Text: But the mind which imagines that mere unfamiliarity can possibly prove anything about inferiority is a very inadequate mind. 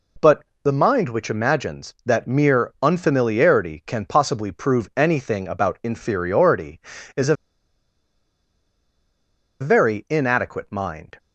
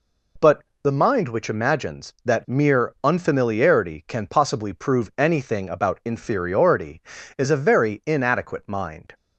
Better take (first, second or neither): second